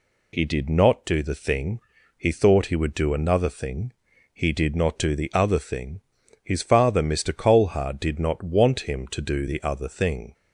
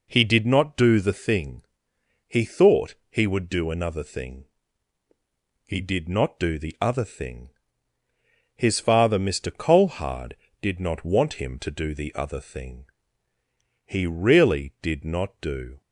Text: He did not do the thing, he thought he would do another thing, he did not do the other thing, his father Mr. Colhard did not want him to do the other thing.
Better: first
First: none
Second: pauses between "thought" and "he"; slight; at 2.9 s; 0.16 s long // goes on to say "He really did not do"; strong; from 13.8 s on; 1.9 s long

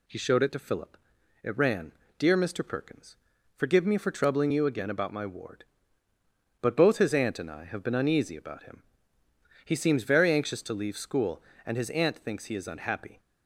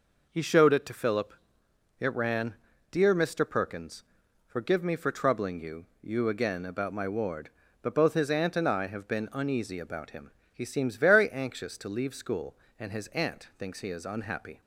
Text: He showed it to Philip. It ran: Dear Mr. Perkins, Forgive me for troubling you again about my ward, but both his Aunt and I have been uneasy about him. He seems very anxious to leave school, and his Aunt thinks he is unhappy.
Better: first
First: none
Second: says "you" twice; at 6.0 s

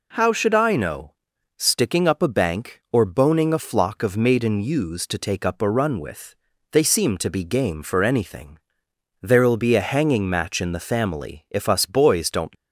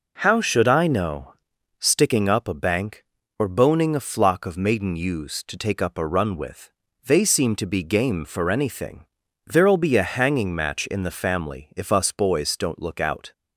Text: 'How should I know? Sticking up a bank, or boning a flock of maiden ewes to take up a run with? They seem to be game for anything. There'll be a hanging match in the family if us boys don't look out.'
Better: second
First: stops before "look out"; at 12.5 s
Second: none

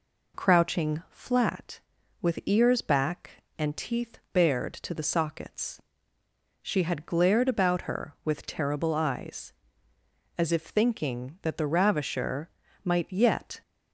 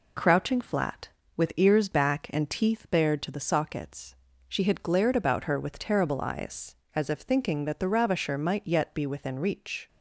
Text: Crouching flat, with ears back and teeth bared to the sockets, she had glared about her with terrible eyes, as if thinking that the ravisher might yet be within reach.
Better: second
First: pauses between "ravisher" and "might"; slight; at 12.4 s; 0.34 s long // stops before "be within reach"; at 13.6 s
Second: none

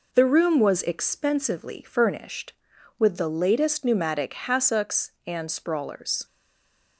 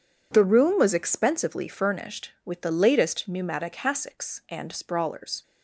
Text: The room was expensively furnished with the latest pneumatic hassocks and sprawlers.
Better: second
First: stays silent after the last word; slight; from 6.2 s on; 0.7 s long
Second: none

